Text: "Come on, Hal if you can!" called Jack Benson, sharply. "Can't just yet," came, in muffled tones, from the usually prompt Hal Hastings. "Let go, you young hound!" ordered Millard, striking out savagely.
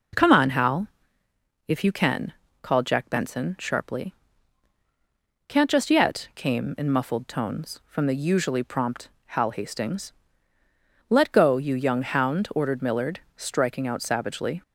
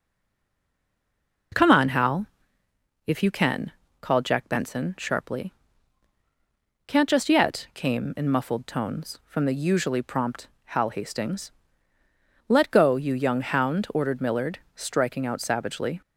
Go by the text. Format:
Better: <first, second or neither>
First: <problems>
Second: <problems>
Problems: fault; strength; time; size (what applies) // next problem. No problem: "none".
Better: first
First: pauses between "Hal" and "if"; noticeable; at 0.8 s; 0.78 s long // pauses between "prompt" and "Hal"; slight; at 9.0 s; 0.20 s long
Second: stays silent before the first word; noticeable; until 1.5 s; 1.5 s long // pauses between "Hal" and "if"; noticeable; at 2.2 s; 0.78 s long // pauses between "prompt" and "Hal"; slight; at 10.4 s; 0.20 s long